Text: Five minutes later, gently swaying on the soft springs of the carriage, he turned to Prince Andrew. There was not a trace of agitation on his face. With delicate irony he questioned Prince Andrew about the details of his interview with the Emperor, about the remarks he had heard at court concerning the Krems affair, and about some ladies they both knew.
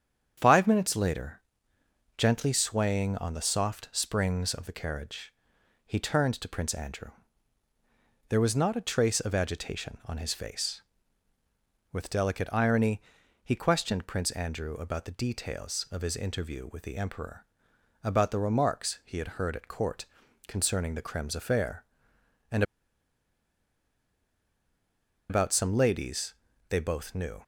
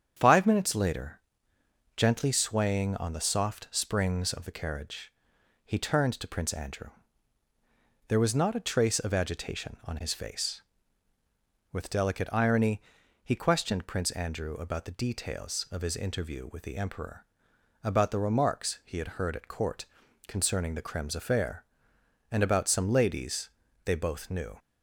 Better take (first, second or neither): second